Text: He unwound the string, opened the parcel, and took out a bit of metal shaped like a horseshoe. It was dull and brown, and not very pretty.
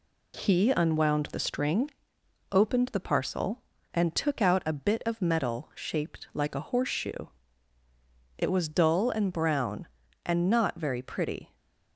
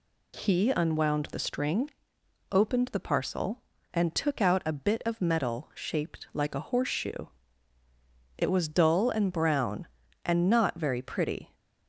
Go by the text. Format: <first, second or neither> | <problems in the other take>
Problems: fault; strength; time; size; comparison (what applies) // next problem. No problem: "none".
second | gets quieter; slight; throughout; 3.5 dB